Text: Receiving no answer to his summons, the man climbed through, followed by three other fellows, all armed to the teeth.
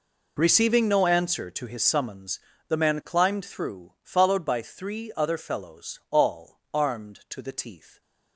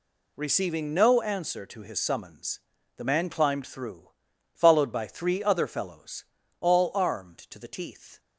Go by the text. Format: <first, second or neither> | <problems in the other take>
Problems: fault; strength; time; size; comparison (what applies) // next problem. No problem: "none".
neither | none